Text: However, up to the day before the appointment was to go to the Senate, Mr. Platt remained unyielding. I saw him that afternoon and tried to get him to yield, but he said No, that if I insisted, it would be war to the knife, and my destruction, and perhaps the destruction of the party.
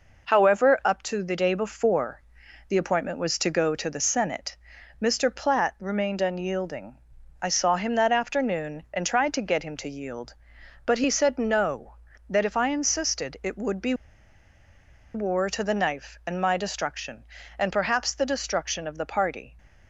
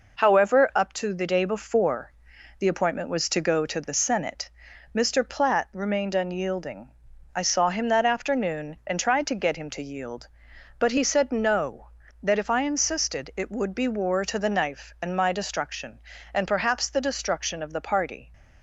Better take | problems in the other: second | pauses between "before" and "the"; noticeable; at 2.1 s; 0.50 s long; noticeable in the second // pauses between "be" and "war"; at 13.9 s; 1.2 s long

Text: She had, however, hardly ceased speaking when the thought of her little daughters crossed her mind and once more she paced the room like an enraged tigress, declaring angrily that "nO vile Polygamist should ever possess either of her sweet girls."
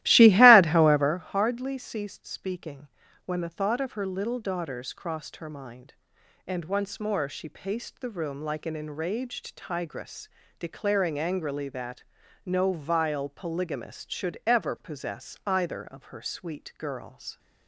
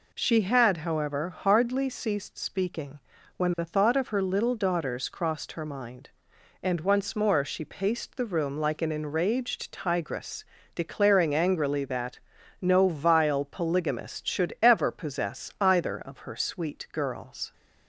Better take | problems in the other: second | starts louder than the rest; strong; until 1.3 s; 15.5 dB // pauses between "speaking" and "when"; at 2.8 s; 0.40 s long; also in the second // pauses between "that" and "nO"; at 12.0 s; 0.44 s long; also in the second

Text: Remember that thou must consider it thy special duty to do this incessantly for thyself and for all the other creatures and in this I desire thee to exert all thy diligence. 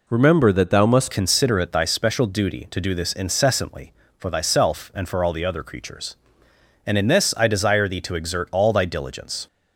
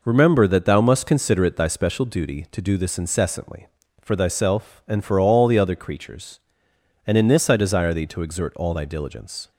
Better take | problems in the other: second | changes voice at "consider"; from 1.1 s on; 8.3 s long

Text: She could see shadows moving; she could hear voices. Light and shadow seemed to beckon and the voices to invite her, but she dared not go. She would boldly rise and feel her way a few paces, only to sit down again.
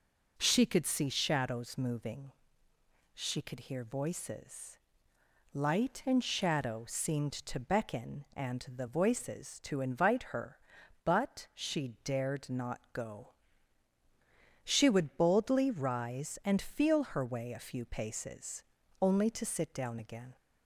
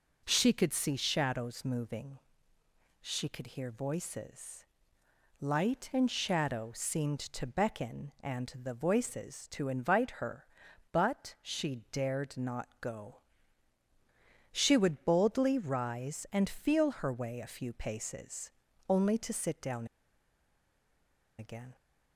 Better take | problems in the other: first | pauses between "down" and "again"; strong; at 19.8 s; 1.5 s long

